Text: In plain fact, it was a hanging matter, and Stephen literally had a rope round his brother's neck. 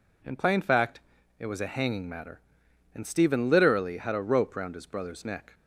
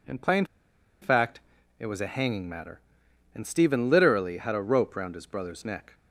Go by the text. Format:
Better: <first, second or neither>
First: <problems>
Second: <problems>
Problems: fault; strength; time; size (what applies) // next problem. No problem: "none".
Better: first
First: none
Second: pauses between "plain" and "fact"; noticeable; at 0.4 s; 0.56 s long